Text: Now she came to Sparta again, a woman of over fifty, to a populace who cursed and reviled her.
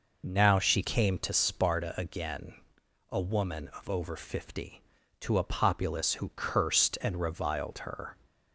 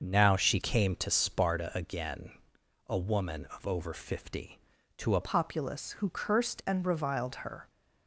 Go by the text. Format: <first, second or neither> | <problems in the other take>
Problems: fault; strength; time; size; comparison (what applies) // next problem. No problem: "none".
first | starts louder than the rest; noticeable; until 1.0 s; 6 dB // changes voice at "populace"; from 5.2 s on; 2.4 s long